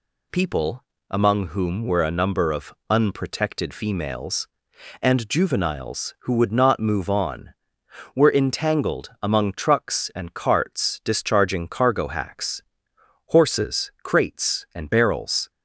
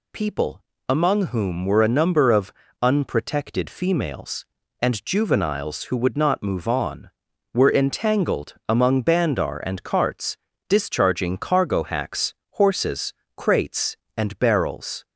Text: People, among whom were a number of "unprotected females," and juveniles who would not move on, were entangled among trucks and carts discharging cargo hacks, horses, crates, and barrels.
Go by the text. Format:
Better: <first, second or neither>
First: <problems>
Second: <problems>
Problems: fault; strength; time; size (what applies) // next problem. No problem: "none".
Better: first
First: pauses between "of" and "unprotected"; slight; at 2.7 s; 0.16 s long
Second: pauses between "of" and "unprotected"; slight; at 2.5 s; 0.28 s long // says "bandar" for "trucks"; at 9.0 s // pauses between "carts" and "discharging"; slight; at 10.3 s; 0.32 s long